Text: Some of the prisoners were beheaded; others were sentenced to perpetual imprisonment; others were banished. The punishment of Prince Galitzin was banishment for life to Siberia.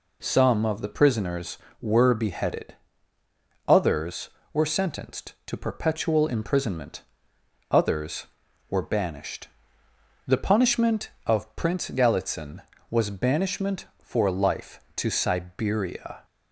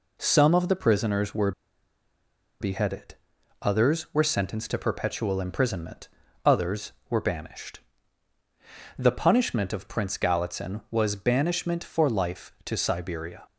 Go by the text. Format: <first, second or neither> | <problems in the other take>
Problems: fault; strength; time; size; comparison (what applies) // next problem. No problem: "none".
first | pauses between "were" and "beheaded"; at 1.5 s; 1.0 s long